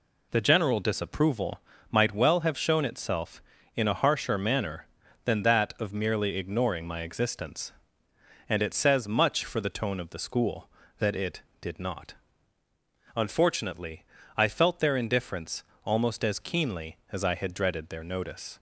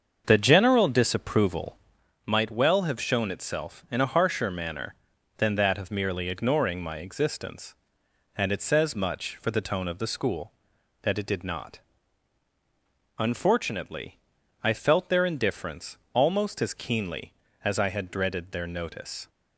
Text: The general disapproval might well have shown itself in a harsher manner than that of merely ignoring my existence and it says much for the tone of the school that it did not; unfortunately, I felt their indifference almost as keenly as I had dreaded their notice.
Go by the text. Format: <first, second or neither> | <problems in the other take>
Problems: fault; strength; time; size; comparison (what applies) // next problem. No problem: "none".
first | starts louder than the rest; until 2.2 s; 7 dB // pauses between "disapproval" and "might"; noticeable; at 1.7 s; 0.48 s long; slight in the first // pauses between "indifference" and "almost"; slight; at 15.9 s; 0.16 s long; slight in the first